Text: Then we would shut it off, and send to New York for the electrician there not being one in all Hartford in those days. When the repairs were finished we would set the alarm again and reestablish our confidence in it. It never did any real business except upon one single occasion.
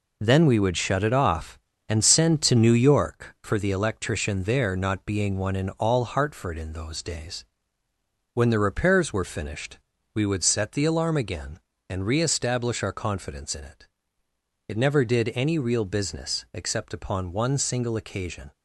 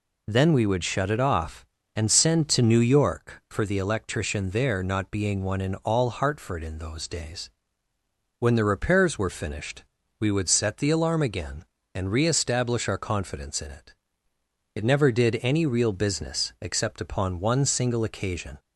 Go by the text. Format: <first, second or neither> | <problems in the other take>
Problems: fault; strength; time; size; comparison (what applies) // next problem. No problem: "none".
second | gets quieter; throughout; 6 dB // pauses between "finished" and "we"; slight; at 9.7 s; 0.36 s long; slight in the second